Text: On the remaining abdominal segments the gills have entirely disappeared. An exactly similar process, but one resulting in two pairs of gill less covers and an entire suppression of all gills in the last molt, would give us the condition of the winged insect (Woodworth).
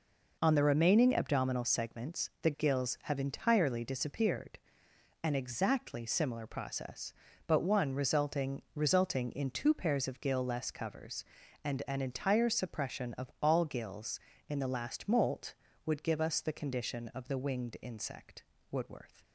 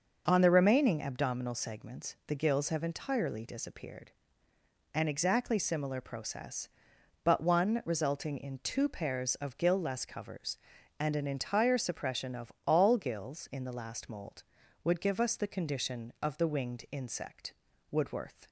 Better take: second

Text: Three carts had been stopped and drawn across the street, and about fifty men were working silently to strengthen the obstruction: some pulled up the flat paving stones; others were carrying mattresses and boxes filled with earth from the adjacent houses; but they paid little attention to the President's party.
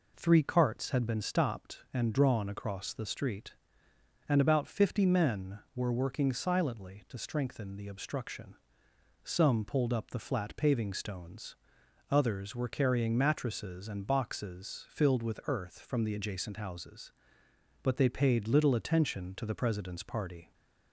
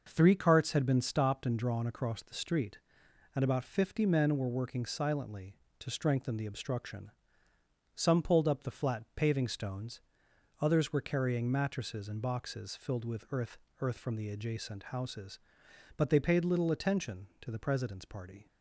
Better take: first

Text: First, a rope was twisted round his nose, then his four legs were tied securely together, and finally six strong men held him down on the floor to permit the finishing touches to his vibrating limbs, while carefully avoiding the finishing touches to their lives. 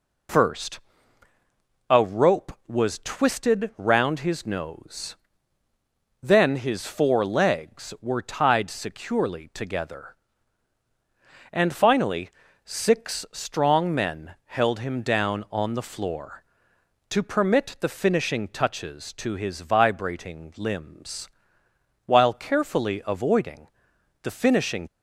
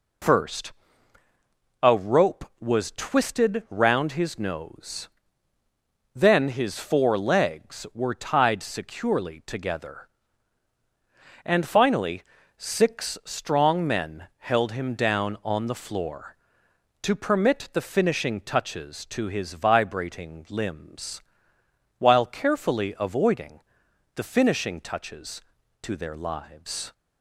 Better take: second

